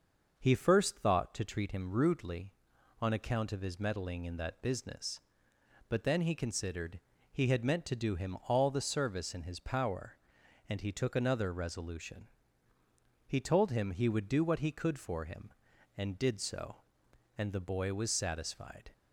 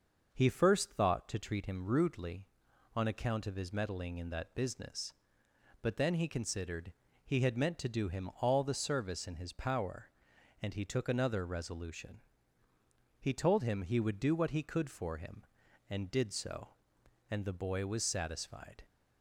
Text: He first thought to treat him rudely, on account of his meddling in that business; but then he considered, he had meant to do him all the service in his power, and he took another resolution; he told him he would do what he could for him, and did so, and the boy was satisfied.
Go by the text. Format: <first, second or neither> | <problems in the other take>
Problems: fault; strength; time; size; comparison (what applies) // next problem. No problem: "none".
neither | starts louder than the rest; noticeable; the same in both